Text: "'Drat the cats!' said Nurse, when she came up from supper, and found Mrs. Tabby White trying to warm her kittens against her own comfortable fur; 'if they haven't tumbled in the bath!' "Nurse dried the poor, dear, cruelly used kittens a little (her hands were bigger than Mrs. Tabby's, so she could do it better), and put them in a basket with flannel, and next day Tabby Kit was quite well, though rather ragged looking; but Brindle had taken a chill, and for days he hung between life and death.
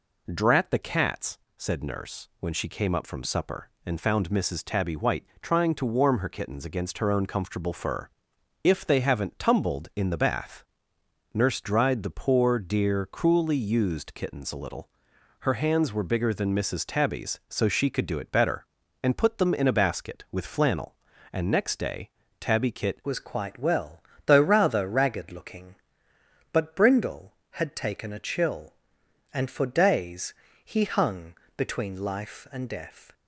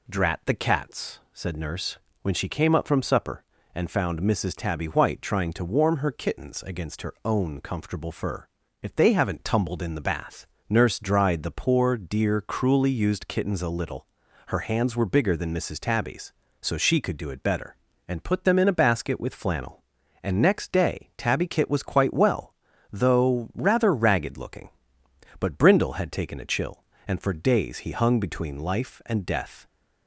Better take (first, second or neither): second